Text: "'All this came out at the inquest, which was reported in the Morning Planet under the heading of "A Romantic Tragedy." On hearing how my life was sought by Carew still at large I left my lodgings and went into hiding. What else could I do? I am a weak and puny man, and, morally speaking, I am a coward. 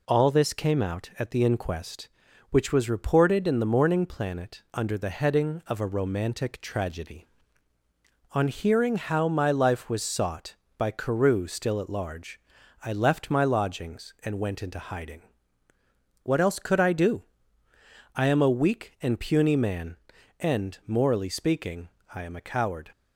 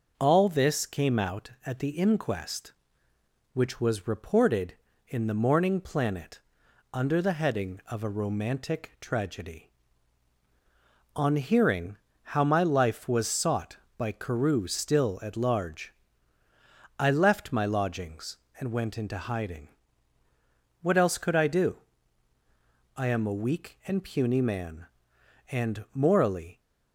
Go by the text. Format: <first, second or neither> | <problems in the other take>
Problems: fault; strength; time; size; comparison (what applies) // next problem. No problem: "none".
first | pauses between "Planet" and "under"; noticeable; at 6.3 s; 0.54 s long // pauses between "hearing" and "how"; slight; at 11.9 s; 0.26 s long // pauses between "large" and "I"; at 15.9 s; 1.0 s long; also in the first // stops before "speaking I am a coward"; at 26.6 s